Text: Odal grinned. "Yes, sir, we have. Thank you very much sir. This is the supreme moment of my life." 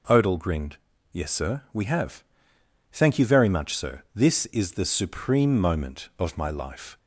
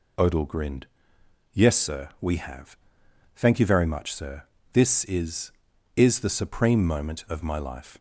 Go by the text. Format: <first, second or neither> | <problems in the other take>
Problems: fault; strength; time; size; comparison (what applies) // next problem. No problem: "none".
first | says "is" twice; at 5.9 s